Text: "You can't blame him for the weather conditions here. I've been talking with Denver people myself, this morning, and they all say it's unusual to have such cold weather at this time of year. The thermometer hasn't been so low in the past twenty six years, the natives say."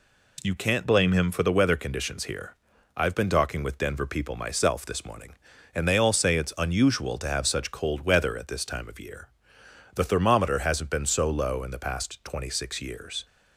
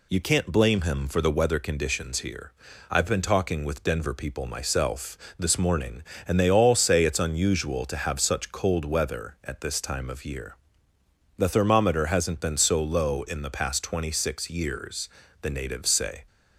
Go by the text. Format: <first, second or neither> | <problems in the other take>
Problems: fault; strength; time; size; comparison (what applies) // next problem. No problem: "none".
second | stops before "the natives say"; at 13.2 s